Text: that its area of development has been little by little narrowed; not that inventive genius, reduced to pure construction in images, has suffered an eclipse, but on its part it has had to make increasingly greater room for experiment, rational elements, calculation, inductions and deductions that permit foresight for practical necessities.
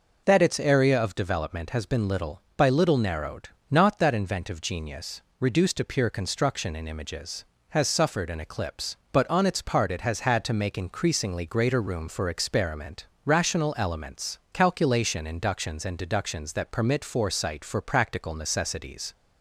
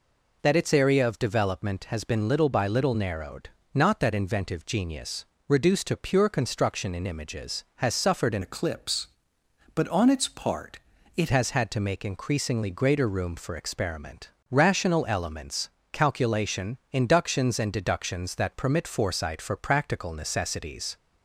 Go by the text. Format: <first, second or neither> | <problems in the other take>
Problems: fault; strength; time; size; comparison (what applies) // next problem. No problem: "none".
first | changes voice from "eclipse" to "it"; from 8.4 to 11.2 s; 2.8 s long // pauses between "part" and "it"; at 10.7 s; 0.38 s long